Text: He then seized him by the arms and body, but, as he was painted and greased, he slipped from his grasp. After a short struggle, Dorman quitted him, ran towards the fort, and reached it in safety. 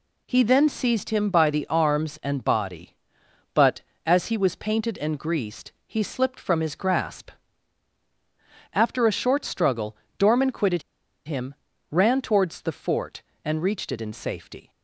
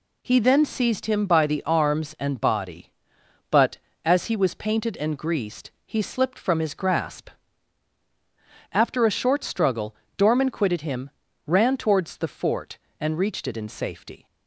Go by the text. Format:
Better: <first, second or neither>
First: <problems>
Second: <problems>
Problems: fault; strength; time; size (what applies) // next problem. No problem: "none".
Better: second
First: pauses between "quitted" and "him"; at 10.8 s; 0.43 s long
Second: none